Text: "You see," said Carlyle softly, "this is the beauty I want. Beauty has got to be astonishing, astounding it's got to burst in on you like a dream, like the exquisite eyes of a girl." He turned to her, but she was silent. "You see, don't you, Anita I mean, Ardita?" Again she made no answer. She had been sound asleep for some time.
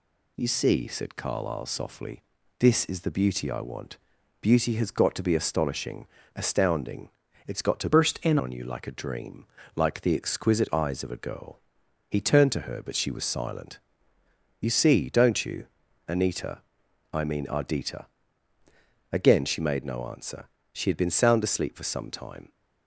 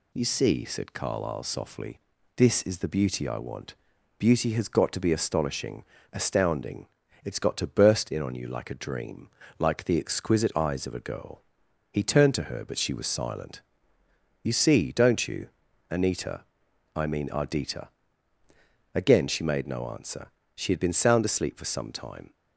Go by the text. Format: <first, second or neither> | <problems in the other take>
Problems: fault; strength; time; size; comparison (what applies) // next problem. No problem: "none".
second | pauses between "astounding" and "it's"; at 7.0 s; 0.38 s long; also in the second // changes voice from "burst" to "in"; from 7.9 to 8.3 s; 0.4 s long // pauses between "Anita" and "I"; noticeable; at 16.6 s; 0.52 s long; noticeable in the second